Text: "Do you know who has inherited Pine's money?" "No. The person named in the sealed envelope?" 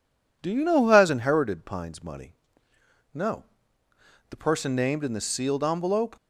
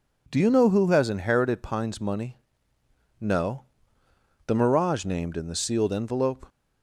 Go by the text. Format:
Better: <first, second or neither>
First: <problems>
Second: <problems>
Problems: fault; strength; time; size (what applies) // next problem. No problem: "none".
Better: first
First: none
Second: says "mirage" for "person"; at 4.5 s